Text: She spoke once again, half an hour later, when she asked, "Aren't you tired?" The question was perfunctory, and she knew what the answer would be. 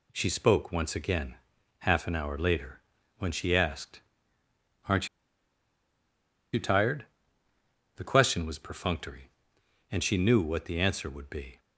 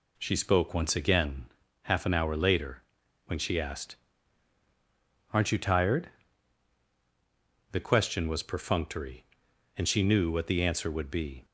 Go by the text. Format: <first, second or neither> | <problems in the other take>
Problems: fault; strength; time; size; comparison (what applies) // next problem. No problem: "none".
second | pauses between "Aren't" and "you"; strong; at 5.0 s; 1.4 s long